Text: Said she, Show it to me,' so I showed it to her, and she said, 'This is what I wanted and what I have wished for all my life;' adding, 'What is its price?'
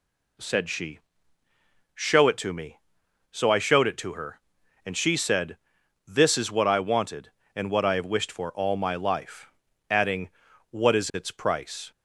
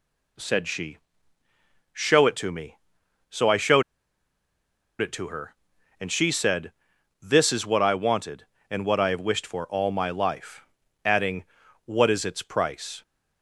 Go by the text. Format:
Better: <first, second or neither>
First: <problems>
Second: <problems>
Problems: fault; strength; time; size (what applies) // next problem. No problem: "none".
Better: first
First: none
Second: pauses between "showed" and "it"; at 3.8 s; 1.1 s long